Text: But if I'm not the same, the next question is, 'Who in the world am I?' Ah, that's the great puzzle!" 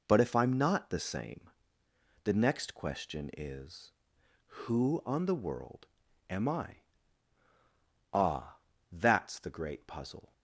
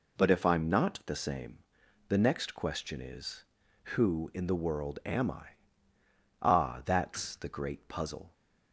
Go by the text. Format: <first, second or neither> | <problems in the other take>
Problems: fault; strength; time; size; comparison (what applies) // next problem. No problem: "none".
second | says "on" for "in"; at 5.0 s // pauses between "world" and "am"; at 5.8 s; 0.42 s long